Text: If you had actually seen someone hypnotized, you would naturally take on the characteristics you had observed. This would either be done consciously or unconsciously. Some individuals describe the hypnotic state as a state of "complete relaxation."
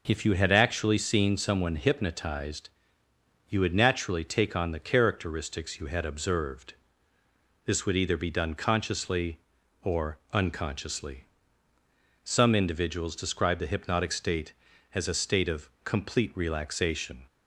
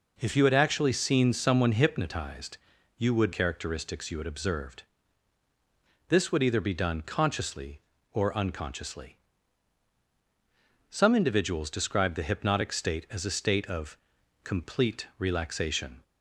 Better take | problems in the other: first | skips "naturally take on the"; at 3.3 s // pauses between "of" and "complete"; noticeable; at 13.9 s; 0.46 s long

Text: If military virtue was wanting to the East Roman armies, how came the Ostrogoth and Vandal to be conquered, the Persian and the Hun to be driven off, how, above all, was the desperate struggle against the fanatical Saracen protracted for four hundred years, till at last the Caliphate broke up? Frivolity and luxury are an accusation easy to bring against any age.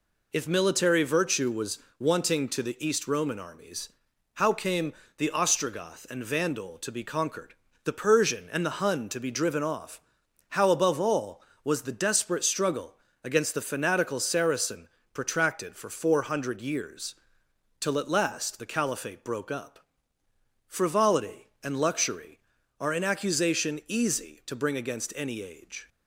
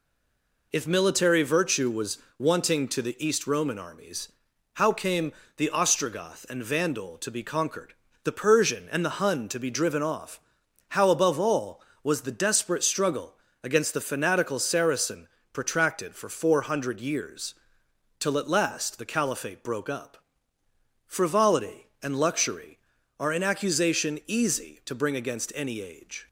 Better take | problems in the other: first | stays silent before the first word; slight; until 0.7 s; 0.7 s long // pauses between "was" and "wanting"; slight; at 2.1 s; 0.20 s long; slight in the first // pauses between "came" and "the"; slight; at 5.3 s; 0.26 s long; slight in the first // pauses between "struggle" and "against"; slight; at 13.3 s; 0.28 s long; slight in the first // pauses between "Saracen" and "protracted"; slight; at 15.2 s; 0.26 s long; slight in the first

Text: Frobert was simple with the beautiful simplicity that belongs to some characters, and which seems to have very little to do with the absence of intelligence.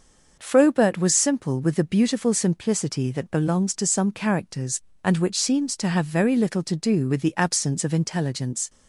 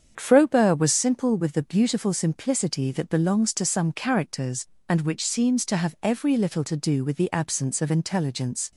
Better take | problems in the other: first | starts louder than the rest; strong; until 1.1 s; 7.5 dB; noticeable in the first // says "every" for "very"; at 6.0 s

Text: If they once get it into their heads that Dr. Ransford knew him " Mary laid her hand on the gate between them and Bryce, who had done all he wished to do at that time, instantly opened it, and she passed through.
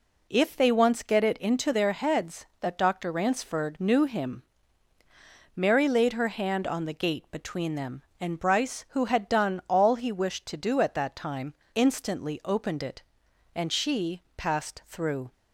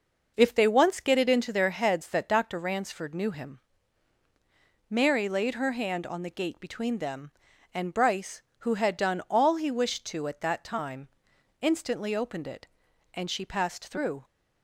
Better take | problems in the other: first | skips "do"; at 10.2 s

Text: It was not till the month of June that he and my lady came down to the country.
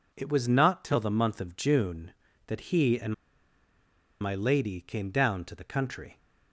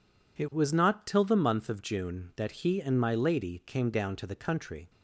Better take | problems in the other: second | pauses between "and" and "my"; at 3.1 s; 1.0 s long

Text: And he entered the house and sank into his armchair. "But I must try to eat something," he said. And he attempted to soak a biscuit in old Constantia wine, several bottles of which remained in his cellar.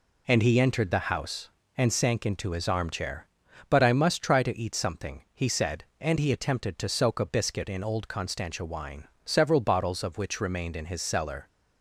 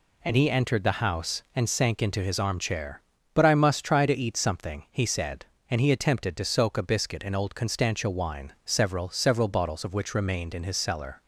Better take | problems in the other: first | says "several" twice; at 9.0 s

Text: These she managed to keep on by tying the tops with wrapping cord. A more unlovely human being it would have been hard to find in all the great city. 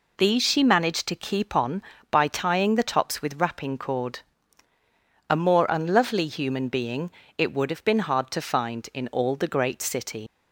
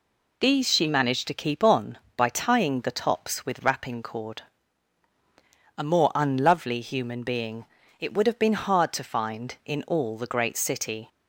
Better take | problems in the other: second | pauses between "being" and "it"; slight; at 7.0 s; 0.28 s long; slight in the second // leaves "city" unfinished; at 10.2 s; 60 ms

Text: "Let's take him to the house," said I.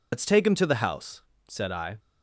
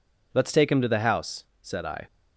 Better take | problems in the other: second | loses the start of "Let's"; at 0.1 s; 115 ms

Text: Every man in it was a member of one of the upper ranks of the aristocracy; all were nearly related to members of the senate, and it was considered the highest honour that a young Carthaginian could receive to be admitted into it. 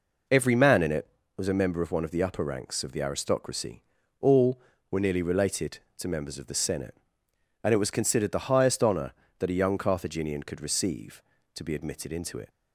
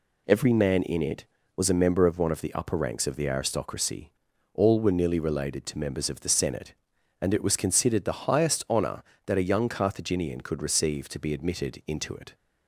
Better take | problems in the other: neither | none

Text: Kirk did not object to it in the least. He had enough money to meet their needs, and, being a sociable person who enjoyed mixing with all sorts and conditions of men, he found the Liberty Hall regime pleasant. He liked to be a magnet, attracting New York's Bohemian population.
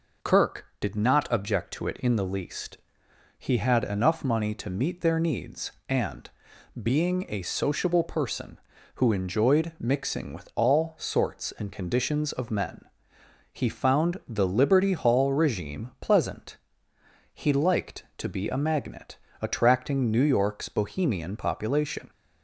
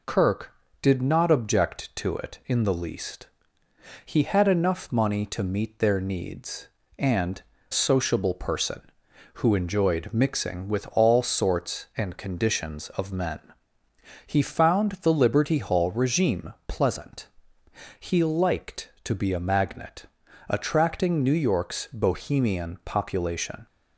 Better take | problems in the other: first | skips "being a"; at 7.5 s

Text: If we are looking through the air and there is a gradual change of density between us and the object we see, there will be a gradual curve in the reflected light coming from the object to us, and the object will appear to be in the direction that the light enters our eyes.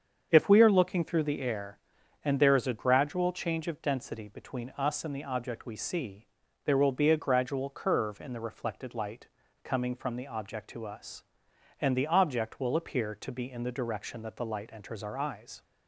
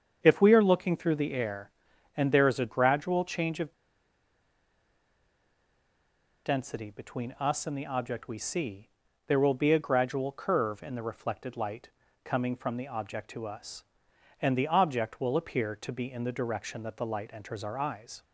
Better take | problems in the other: first | starts louder than the rest; strong; until 1.2 s; 7.5 dB; strong in the first // pauses between "of" and "density"; strong; at 3.7 s; 2.7 s long // pauses between "light" and "coming"; at 11.8 s; 0.38 s long; also in the first

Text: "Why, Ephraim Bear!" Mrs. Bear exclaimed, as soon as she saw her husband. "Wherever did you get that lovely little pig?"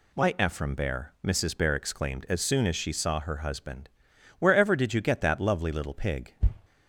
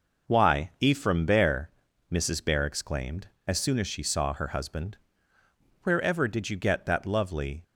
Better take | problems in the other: first | stops before "little pig"; at 7.6 s

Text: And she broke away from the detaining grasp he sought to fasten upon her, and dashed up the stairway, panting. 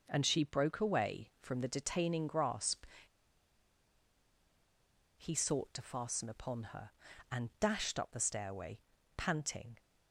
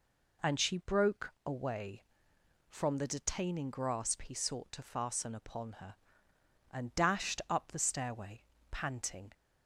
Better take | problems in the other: second | pauses between "grasp" and "he"; strong; at 2.8 s; 2.3 s long

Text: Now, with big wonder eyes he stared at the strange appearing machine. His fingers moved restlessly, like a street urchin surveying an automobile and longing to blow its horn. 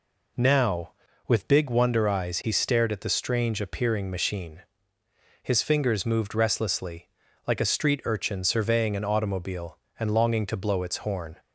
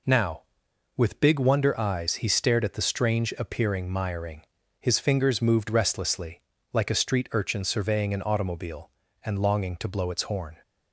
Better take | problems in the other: first | says "miring" for "machine"; at 3.8 s

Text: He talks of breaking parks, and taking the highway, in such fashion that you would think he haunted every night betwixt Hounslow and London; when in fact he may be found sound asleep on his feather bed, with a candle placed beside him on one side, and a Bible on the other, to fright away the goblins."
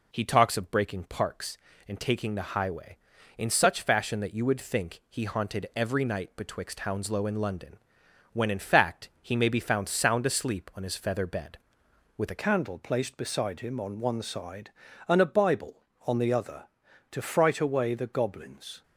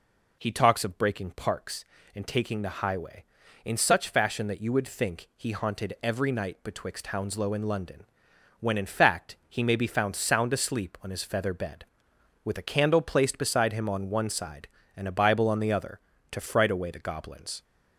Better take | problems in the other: second | changes voice at "candle"; from 12.3 s on; 6.5 s long

